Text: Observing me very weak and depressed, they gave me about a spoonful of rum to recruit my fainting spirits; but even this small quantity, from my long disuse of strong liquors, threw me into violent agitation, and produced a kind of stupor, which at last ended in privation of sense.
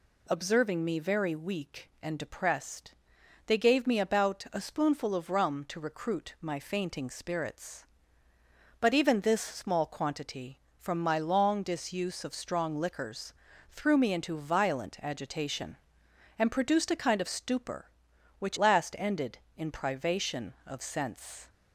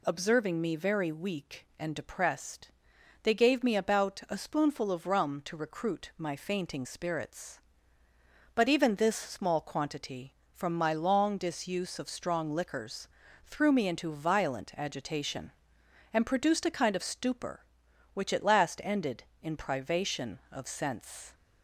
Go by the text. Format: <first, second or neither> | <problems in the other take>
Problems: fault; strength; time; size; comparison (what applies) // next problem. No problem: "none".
second | skips "at"; at 18.5 s